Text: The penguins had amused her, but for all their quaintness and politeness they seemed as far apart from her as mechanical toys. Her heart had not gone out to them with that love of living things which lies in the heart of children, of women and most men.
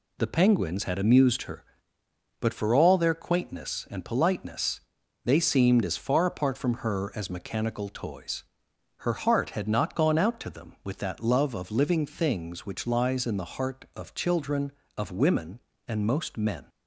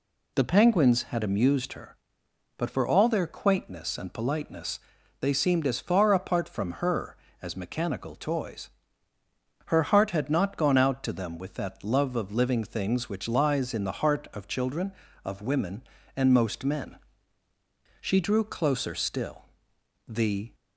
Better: first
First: pauses between "politeness" and "they"; at 4.7 s; 0.44 s long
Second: pauses between "politeness" and "they"; at 4.8 s; 0.40 s long // goes on to say "She drew closer still The"; strong; from 18.0 s on; 2.5 s long

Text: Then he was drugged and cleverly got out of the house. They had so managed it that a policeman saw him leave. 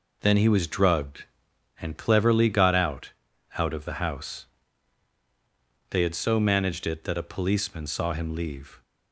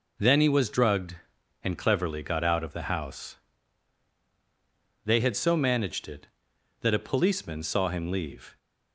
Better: second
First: says "out" twice; at 3.5 s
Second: none

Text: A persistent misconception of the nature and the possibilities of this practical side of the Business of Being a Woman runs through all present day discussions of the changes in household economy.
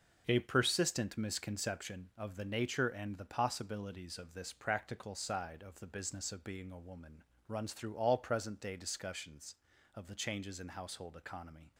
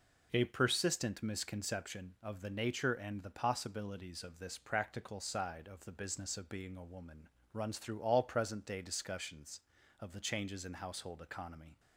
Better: second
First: gets quieter; strong; throughout; 9 dB // pauses between "Woman" and "runs"; slight; at 7.2 s; 0.24 s long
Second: pauses between "Woman" and "runs"; slight; at 7.2 s; 0.24 s long

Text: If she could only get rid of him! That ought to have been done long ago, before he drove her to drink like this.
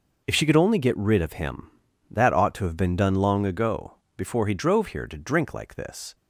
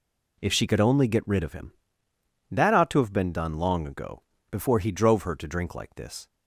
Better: second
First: says "here" for "her"; at 4.8 s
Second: none

